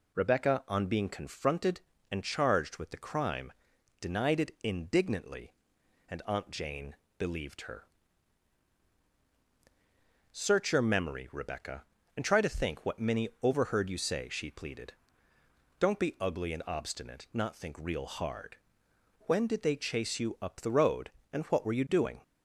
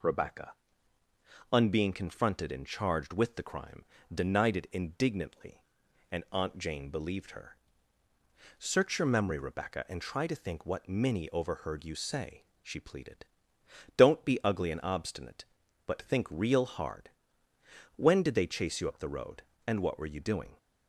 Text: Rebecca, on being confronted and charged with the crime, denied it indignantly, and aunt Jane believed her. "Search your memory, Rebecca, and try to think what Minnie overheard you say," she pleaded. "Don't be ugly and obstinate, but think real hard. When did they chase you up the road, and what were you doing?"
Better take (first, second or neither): second